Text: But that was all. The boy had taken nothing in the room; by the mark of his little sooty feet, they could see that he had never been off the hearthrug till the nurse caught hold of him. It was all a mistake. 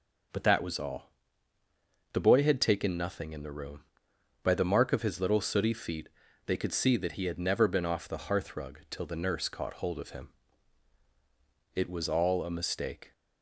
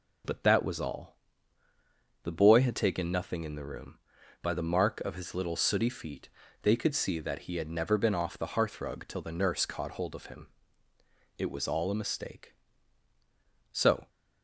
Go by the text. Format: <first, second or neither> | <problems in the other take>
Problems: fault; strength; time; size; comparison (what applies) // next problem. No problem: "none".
first | goes on to say "So"; slight; from 13.7 s on; 0.36 s long